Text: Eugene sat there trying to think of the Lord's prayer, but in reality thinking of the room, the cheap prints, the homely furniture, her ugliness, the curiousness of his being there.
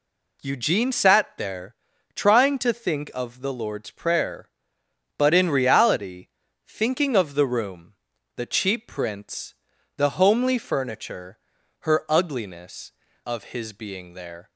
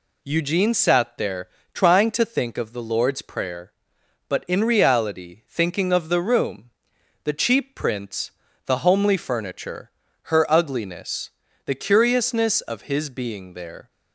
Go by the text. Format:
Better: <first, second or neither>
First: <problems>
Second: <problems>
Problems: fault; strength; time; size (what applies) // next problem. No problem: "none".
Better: second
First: pauses between "there" and "trying"; at 1.7 s; 0.40 s long // pauses between "reality" and "thinking"; at 6.2 s; 0.40 s long // skips "the curiousness"; at 13.0 s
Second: pauses between "there" and "trying"; slight; at 1.4 s; 0.26 s long